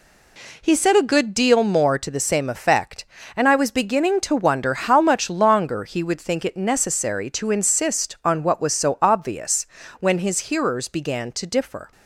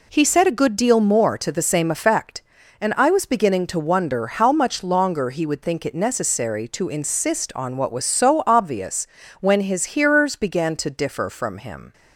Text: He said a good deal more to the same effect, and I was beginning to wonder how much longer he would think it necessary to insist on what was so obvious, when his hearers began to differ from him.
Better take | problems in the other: second | stops before "from him"; at 11.9 s

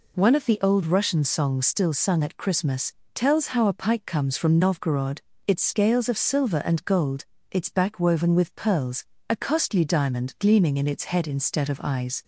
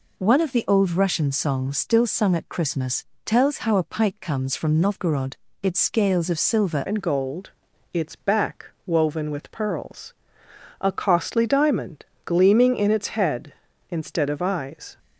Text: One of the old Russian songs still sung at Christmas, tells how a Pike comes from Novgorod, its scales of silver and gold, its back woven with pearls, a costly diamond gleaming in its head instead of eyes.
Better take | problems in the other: first | changes voice at "and"; from 6.8 s on; 8.1 s long // pauses between "back" and "woven"; slight; at 8.6 s; 0.20 s long // pauses between "diamond" and "gleaming"; slight; at 12.0 s; 0.22 s long

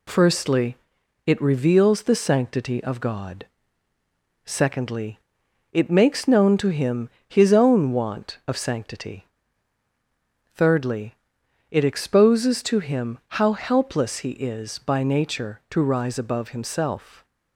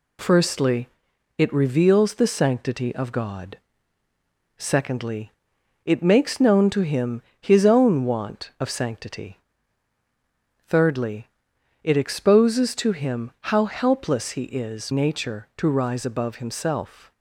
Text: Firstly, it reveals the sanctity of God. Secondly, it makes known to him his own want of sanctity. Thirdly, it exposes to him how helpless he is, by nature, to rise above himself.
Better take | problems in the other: first | pauses between "him" and "his"; slight; at 7.2 s; 0.18 s long; slight in the first // skips "by"; at 14.9 s

